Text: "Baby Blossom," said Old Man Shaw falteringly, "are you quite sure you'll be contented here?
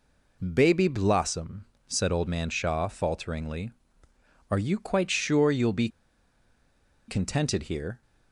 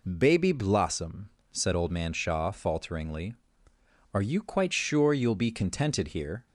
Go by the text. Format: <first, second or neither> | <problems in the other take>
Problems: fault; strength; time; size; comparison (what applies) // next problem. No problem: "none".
second | pauses between "be" and "contented"; at 5.8 s; 1.2 s long